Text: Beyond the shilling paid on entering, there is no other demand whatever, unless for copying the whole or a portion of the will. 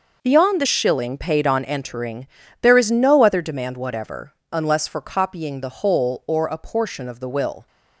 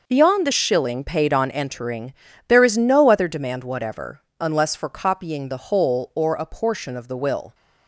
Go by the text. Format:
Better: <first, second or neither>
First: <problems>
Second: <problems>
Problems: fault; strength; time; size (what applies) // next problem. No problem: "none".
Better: neither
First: none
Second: none